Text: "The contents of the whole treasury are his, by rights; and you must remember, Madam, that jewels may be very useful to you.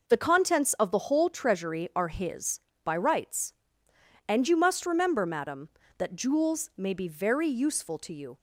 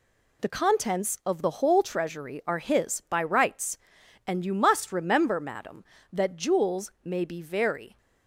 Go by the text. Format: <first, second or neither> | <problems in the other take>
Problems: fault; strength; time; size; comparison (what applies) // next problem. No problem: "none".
first | stops before "useful to you"; at 7.9 s